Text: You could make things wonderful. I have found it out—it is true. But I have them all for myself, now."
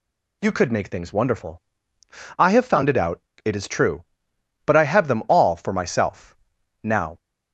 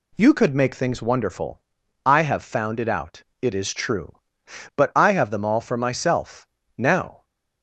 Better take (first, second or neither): neither